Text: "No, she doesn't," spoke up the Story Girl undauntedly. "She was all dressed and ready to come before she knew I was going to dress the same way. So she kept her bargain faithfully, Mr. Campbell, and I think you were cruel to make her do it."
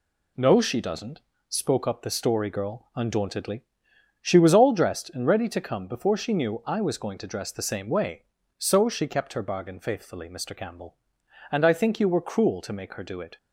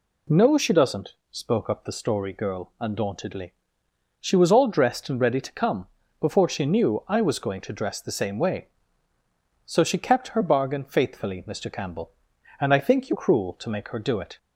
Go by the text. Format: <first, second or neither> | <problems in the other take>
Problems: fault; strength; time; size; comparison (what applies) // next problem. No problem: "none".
first | pauses between "come" and "before"; slight; at 5.8 s; 0.34 s long // skips "were"; at 13.1 s